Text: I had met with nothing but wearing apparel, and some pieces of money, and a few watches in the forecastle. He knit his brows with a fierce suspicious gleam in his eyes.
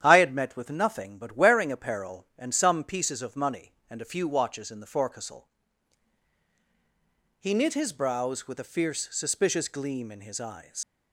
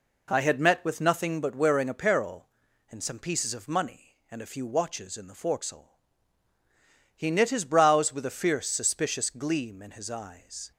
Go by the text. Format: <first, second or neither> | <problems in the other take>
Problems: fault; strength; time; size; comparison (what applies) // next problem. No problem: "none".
second | starts louder than the rest; strong; until 1.0 s; 10 dB // leaves "eyes" unfinished; at 10.8 s; 95 ms